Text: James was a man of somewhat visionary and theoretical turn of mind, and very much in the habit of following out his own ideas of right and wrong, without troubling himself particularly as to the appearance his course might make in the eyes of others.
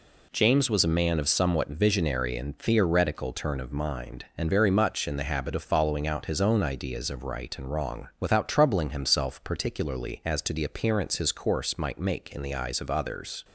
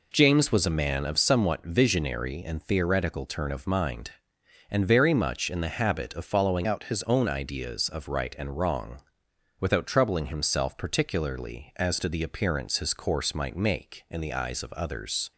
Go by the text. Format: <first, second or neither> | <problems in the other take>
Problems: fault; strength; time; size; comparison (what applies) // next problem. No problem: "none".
first | changes voice from "out" to "his"; from 6.6 to 7.0 s; 0.4 s long